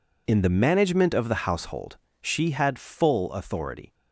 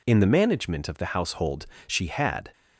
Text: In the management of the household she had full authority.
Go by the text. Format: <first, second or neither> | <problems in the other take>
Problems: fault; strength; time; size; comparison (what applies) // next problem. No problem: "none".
first | pauses between "household" and "she"; slight; at 1.6 s; 0.22 s long; slight in the first // stops before "full authority"; at 2.5 s